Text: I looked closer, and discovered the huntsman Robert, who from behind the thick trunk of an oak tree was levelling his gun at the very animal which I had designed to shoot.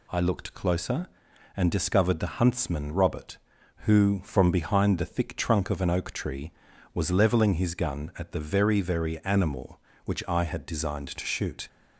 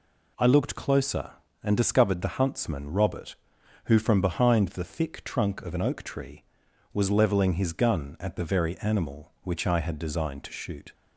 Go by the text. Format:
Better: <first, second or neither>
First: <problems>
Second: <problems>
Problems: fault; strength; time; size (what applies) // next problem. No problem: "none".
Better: second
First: says "very" twice; at 8.8 s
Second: none